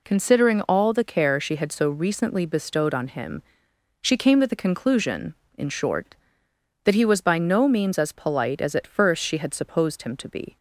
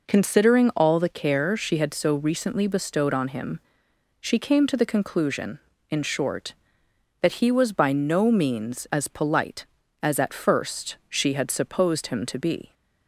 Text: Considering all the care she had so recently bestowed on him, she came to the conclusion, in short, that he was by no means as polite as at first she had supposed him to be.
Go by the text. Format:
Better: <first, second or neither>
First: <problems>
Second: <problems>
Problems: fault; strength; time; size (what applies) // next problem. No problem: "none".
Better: neither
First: none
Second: none